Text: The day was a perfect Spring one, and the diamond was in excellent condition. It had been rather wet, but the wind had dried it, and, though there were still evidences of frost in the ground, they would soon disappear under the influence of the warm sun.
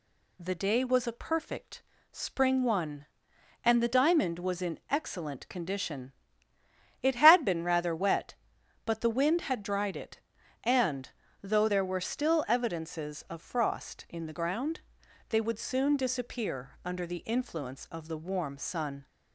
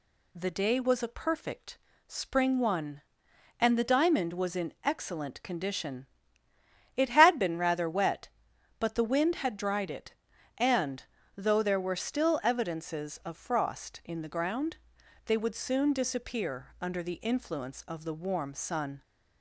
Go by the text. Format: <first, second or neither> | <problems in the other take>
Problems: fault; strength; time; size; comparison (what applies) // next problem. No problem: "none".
neither | pauses between "perfect" and "Spring"; slight; the same in both